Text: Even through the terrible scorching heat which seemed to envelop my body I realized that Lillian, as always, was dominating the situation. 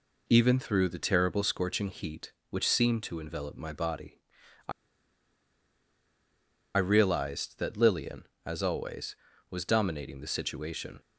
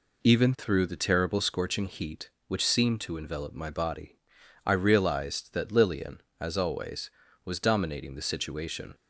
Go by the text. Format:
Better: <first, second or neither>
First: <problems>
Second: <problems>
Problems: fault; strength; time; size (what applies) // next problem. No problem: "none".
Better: second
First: pauses between "body" and "I"; noticeable; at 4.1 s; 0.50 s long // pauses between "I" and "realized"; strong; at 4.7 s; 2.0 s long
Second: pauses between "body" and "I"; noticeable; at 4.1 s; 0.50 s long